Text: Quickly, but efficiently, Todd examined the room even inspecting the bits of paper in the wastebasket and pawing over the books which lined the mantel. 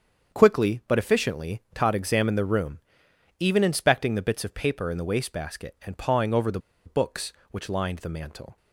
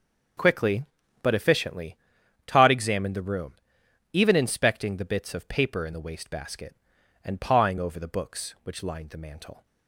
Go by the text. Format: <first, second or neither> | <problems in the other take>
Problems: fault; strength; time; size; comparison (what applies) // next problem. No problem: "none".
second | starts louder than the rest; strong; until 1.4 s; 7 dB; also in the second // pauses between "room" and "even"; noticeable; at 2.7 s; 0.60 s long; noticeable in the second // pauses between "the" and "books"; slight; at 6.5 s; 0.26 s long